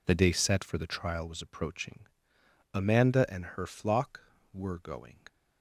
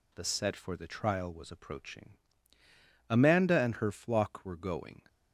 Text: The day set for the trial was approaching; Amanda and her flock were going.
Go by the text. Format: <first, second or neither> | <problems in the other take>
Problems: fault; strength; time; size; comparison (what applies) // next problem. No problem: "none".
first | skips "day"; at 0.2 s